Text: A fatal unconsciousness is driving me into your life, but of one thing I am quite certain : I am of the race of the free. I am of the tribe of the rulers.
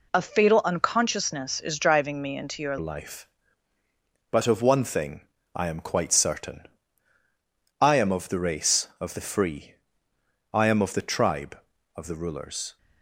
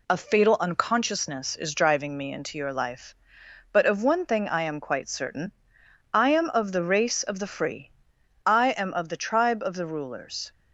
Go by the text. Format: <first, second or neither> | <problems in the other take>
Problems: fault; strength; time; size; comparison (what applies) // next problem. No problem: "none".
second | changes voice at "life"; from 2.7 s on; 10.0 s long // pauses between "thing" and "I"; slight; at 5.1 s; 0.34 s long